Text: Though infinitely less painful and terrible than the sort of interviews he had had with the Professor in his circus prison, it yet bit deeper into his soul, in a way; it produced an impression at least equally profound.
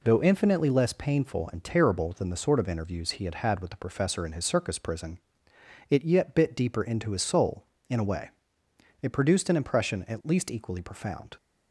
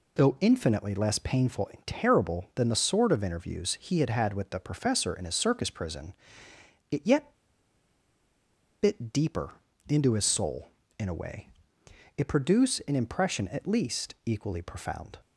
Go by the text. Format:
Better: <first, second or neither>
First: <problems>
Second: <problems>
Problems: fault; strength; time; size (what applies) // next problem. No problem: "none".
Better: first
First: none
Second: pauses between "yet" and "bit"; strong; at 7.3 s; 1.4 s long // pauses between "deeper" and "into"; slight; at 9.5 s; 0.36 s long